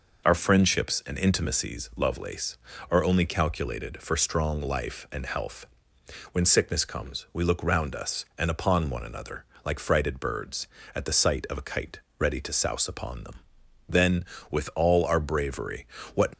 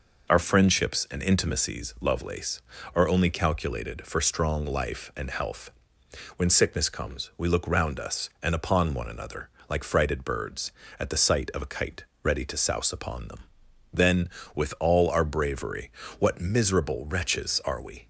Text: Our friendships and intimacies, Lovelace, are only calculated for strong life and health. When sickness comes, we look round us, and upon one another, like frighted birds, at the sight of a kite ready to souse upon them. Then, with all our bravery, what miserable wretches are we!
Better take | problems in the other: second | pauses between "kite" and "ready"; slight; at 11.9 s; 0.20 s long; slight in the second // stops before "miserable wretches are we"; at 16.3 s

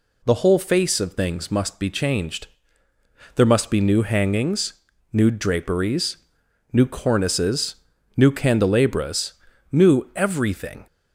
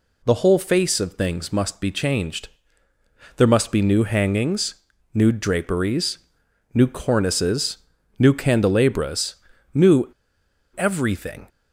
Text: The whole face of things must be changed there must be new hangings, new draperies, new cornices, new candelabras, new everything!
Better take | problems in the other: first | pauses between "changed" and "there"; noticeable; at 2.4 s; 0.88 s long; noticeable in the first // pauses between "new" and "everything"; noticeable; at 10.1 s; 0.65 s long

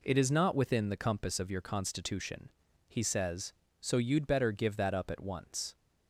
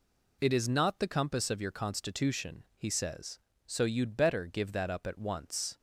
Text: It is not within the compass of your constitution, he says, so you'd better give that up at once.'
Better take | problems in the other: first | skips "within"; at 1.0 s

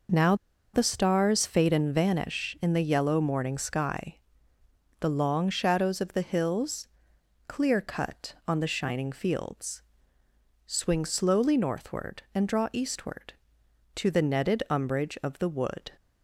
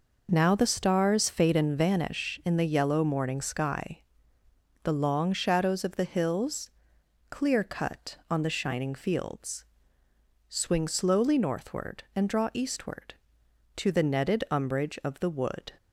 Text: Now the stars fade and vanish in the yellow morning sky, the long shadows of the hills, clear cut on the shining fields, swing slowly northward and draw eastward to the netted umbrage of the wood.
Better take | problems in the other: second | pauses between "Now" and "the"; at 0.3 s; 0.39 s long

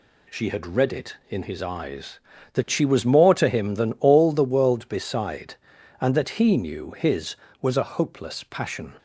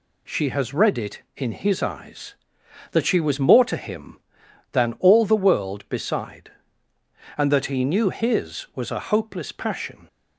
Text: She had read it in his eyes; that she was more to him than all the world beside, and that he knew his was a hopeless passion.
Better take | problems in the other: first | says "has" for "had"; at 0.4 s

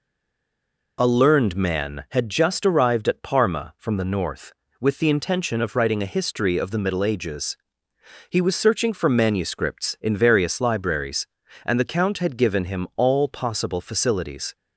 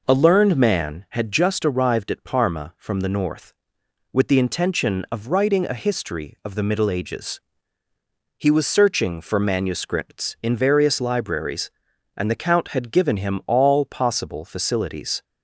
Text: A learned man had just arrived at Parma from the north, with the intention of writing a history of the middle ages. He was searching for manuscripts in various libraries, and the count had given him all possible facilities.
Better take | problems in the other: second | stays silent before the first word; slight; until 0.9 s; 0.9 s long

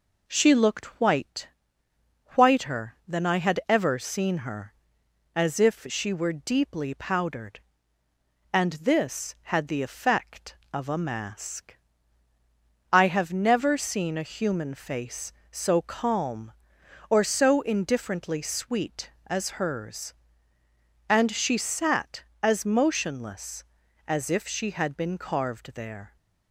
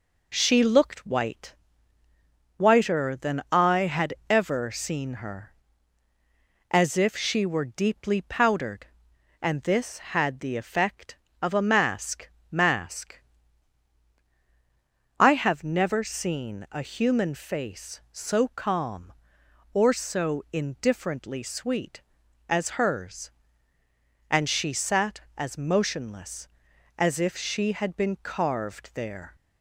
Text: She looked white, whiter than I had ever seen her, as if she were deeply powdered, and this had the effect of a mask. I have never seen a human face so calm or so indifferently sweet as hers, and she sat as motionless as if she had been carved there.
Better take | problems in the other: first | pauses between "had" and "ever"; slight; at 4.1 s; 0.16 s long // says "mask" twice; at 12.5 s

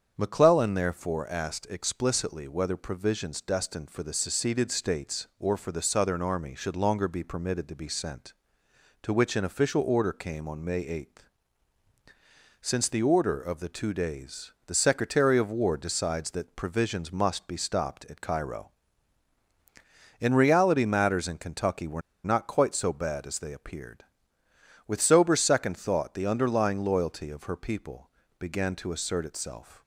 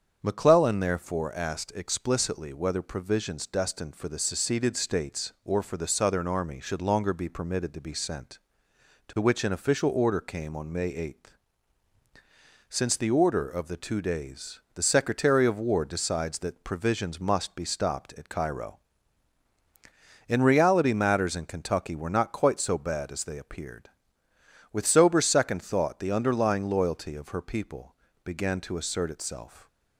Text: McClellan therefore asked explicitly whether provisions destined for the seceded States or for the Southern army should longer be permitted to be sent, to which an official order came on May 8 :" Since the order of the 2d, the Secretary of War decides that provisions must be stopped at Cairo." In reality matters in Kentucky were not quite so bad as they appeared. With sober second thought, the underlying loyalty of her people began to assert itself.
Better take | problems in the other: second | starts louder than the rest; strong; until 1.1 s; 7.5 dB; strong in the second // pauses between "were" and "not"; slight; at 22.0 s; 0.23 s long // pauses between "people" and "began"; slight; at 28.1 s; 0.26 s long; slight in the second

